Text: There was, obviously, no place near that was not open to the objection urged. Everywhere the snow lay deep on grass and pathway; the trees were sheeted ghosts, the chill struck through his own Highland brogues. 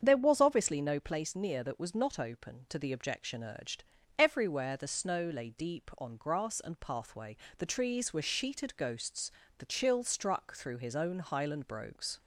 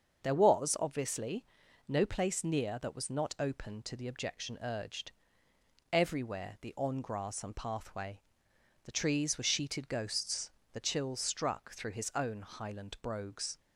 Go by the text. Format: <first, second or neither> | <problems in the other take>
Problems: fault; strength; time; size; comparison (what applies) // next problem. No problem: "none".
first | starts louder than the rest; until 1.2 s; 6.5 dB; strong in the first // skips "snow lay deep"; at 6.7 s